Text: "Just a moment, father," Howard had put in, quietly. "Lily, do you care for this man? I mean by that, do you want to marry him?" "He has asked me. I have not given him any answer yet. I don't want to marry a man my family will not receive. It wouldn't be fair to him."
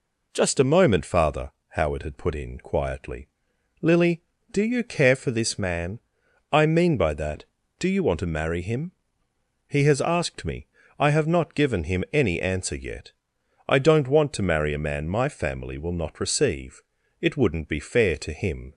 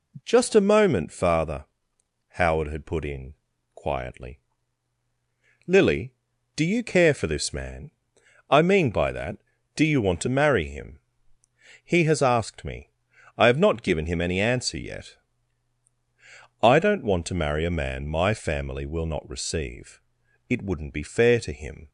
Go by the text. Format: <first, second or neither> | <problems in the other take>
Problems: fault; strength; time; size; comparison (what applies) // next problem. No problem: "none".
neither | none